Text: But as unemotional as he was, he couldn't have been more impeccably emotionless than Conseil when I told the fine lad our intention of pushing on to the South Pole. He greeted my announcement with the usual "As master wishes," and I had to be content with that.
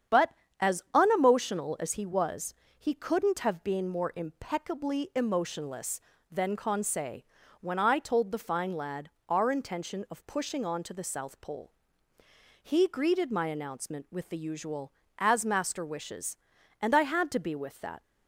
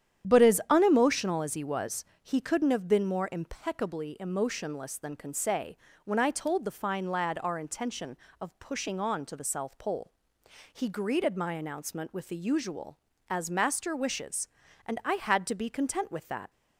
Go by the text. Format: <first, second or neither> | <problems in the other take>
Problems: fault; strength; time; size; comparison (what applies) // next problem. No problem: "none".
second | starts louder than the rest; strong; until 1.5 s; 8.5 dB; strong in the second // pauses between "Conseil" and "when"; at 7.2 s; 0.38 s long; slight in the second // pauses between "lad" and "our"; slight; at 9.0 s; 0.18 s long // skips "content"; at 17.5 s